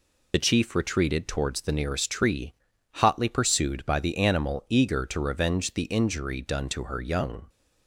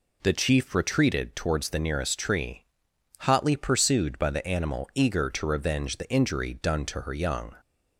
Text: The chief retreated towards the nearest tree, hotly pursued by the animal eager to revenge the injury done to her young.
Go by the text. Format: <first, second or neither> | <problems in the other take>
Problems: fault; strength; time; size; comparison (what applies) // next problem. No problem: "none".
second | loses the start of "The"; at 0.3 s; 35 ms